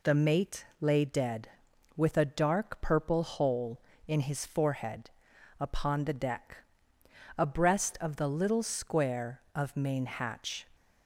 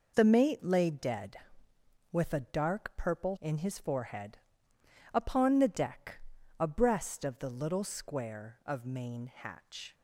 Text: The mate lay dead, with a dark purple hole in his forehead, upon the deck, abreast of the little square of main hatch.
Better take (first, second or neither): first